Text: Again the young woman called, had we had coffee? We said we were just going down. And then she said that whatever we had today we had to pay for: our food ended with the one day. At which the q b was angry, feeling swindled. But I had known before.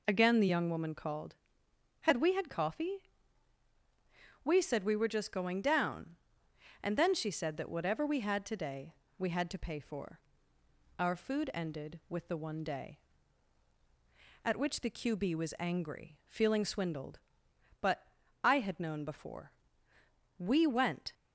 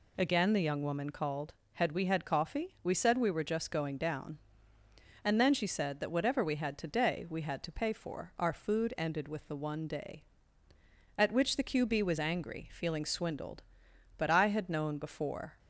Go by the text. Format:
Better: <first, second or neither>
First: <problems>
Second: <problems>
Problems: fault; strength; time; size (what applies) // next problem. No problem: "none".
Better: second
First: pauses between "today" and "we"; slight; at 8.9 s; 0.24 s long // pauses between "But" and "I"; at 18.0 s; 0.38 s long // goes on to say "We went"; noticeable; from 20.3 s on; 0.76 s long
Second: none